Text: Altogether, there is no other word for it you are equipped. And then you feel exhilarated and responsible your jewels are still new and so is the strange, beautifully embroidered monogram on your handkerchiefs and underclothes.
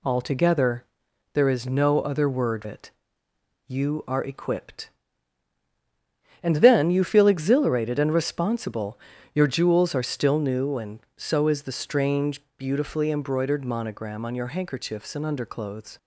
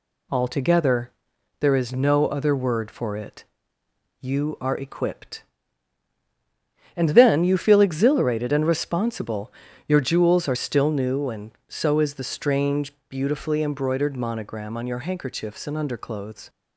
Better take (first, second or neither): second